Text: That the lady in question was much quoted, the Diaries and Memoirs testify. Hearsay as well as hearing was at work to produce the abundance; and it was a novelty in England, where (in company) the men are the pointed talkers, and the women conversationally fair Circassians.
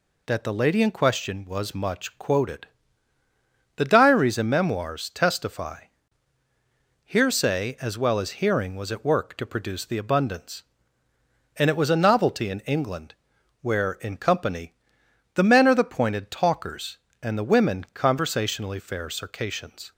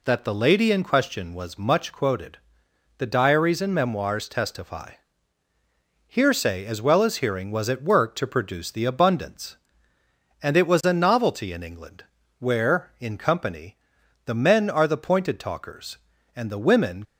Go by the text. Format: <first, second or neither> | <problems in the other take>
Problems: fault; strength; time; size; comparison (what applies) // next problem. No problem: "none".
first | stops before "conversationally fair Circassians"; at 17.0 s